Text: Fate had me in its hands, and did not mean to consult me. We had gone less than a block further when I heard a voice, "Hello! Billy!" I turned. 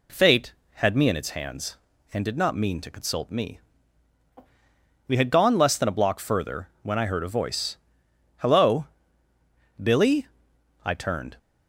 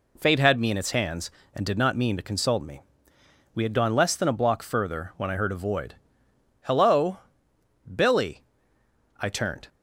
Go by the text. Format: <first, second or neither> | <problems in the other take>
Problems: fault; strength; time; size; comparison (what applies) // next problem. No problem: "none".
first | says "void" for "voice"; at 5.5 s